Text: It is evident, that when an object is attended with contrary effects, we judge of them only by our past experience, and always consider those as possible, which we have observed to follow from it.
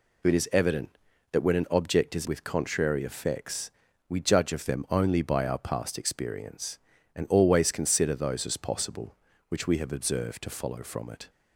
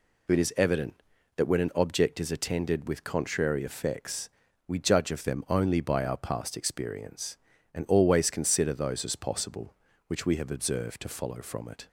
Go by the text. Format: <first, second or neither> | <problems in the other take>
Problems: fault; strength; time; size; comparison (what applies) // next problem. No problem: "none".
second | skips "attended"; at 2.2 s